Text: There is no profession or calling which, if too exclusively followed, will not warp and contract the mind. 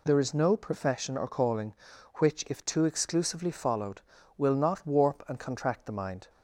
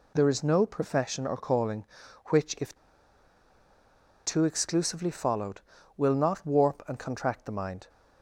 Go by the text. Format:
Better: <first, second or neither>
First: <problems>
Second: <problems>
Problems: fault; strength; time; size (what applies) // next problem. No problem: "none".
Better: first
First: none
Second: pauses between "if" and "too"; strong; at 2.7 s; 1.4 s long